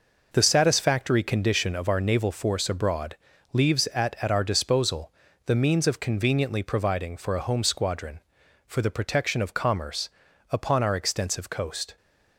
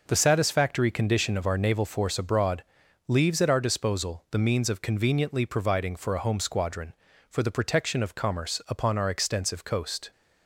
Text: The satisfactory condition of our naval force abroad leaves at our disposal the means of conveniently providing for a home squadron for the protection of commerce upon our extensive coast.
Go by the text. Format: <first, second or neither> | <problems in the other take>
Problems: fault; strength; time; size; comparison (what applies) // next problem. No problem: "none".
second | pauses between "abroad" and "leaves"; slight; at 3.1 s; 0.36 s long; noticeable in the second // says "at" twice; at 4.2 s // pauses between "disposal" and "the"; slight; at 5.1 s; 0.32 s long // pauses between "commerce" and "upon"; at 10.0 s; 0.42 s long